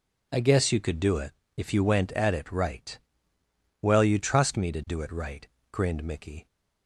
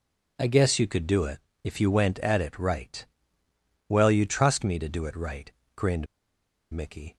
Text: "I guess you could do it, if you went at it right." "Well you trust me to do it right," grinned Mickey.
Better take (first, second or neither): first